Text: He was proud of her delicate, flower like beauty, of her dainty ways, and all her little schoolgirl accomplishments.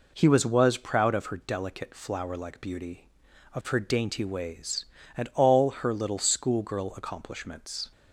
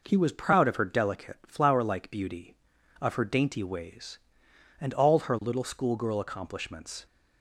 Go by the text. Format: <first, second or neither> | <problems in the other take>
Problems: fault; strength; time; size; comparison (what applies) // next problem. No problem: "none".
second | says "was" twice; at 0.4 s